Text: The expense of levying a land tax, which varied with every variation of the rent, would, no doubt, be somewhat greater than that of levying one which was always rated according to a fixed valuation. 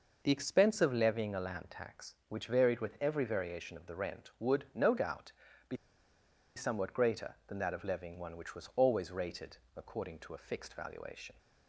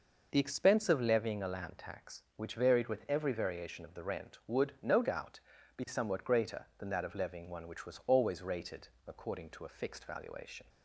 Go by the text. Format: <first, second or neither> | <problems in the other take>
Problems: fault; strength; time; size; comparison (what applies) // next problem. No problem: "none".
second | pauses between "be" and "somewhat"; noticeable; at 5.7 s; 0.80 s long // pauses between "rated" and "according"; slight; at 9.5 s; 0.18 s long; slight in the second